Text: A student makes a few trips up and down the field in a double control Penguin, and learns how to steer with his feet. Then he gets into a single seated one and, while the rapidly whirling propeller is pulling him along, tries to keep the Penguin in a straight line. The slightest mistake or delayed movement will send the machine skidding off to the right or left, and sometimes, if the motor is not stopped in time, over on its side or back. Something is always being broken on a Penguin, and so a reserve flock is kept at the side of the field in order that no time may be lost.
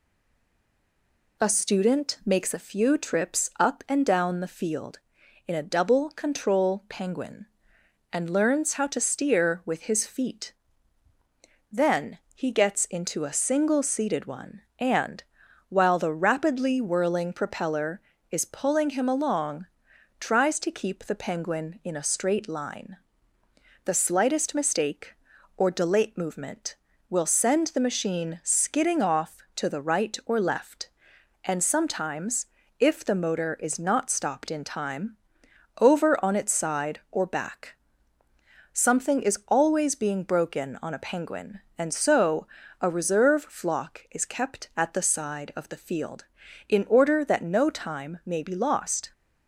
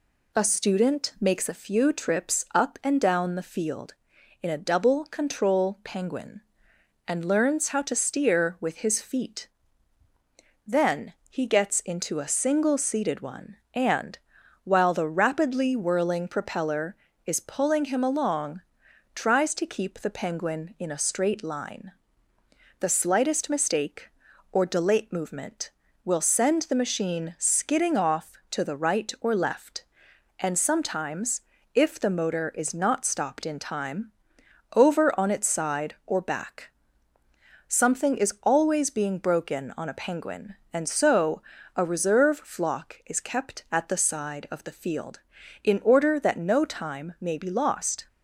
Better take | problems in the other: second | stays silent before the first word; noticeable; until 1.3 s; 1.3 s long // pauses between "Then" and "he"; slight; at 12.1 s; 0.16 s long; slight in the second // pauses between "so" and "a"; slight; at 42.4 s; 0.34 s long; slight in the second

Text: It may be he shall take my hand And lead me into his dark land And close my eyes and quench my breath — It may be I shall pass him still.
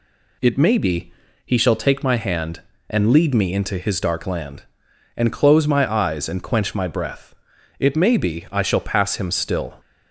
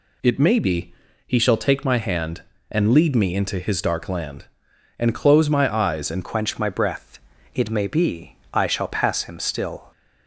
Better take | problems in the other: first | pauses between "be" and "he"; slight; at 0.9 s; 0.32 s long; slight in the first // changes voice at "quench"; from 6.2 s on; 3.7 s long // pauses between "be" and "I"; slight; at 8.3 s; 0.18 s long

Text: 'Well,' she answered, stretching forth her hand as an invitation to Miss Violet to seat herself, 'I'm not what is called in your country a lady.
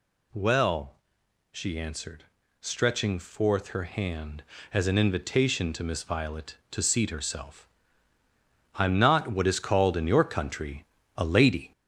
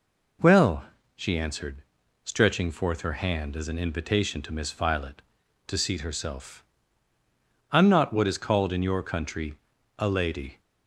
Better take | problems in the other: second | gets louder; noticeable; throughout; 4.5 dB // pauses between "country" and "a"; slight; at 10.8 s; 0.32 s long; also in the second

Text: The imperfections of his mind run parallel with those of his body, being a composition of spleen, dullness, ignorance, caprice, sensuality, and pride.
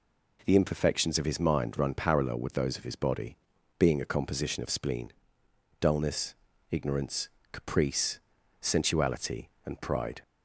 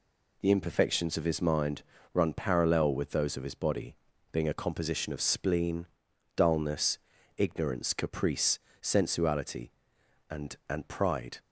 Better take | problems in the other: first | pauses between "mind" and "run"; slight; at 1.8 s; 0.30 s long // says "and" twice; at 10.6 s

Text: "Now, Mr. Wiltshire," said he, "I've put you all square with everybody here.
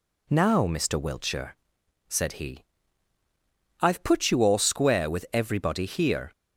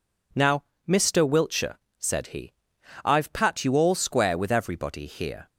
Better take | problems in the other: first | says "pat" for "put"; at 3.3 s

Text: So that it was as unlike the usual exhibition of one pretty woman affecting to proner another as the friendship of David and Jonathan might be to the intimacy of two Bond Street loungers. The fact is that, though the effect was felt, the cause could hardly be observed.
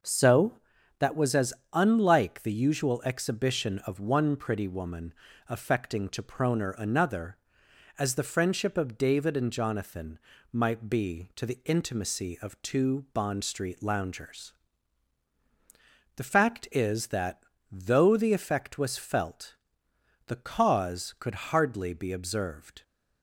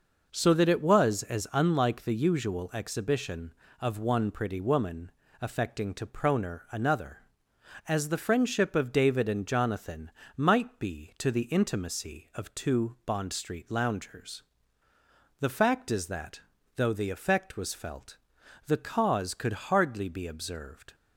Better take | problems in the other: second | skips "it"; at 1.1 s // pauses between "as" and "unlike"; slight; at 1.5 s; 0.20 s long // pauses between "woman" and "affecting"; slight; at 5.1 s; 0.36 s long; slight in the second // pauses between "Jonathan" and "might"; slight; at 10.1 s; 0.34 s long; slight in the second

